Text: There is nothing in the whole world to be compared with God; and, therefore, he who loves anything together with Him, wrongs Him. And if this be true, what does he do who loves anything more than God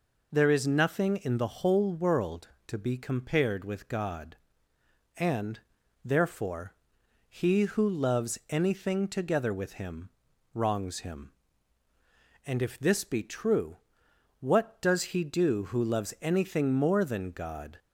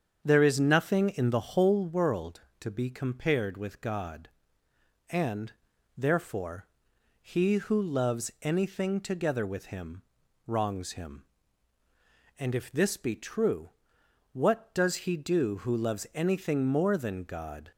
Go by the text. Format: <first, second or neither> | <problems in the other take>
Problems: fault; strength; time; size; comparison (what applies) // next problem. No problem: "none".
first | starts louder than the rest; strong; until 1.9 s; 7.5 dB